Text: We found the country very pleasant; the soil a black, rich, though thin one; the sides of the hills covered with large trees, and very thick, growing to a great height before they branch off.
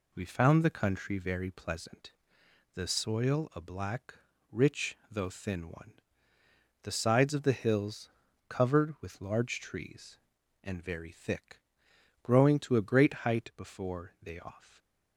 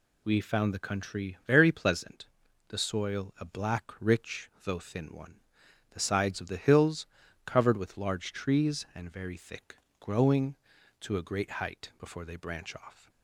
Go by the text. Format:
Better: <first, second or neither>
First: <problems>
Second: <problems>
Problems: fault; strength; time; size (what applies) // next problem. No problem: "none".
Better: second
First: pauses between "hills" and "covered"; at 8.0 s; 0.40 s long // skips "branch"; at 14.4 s // stays silent after the last word; slight; from 14.6 s on; 0.5 s long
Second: pauses between "hills" and "covered"; at 7.0 s; 0.38 s long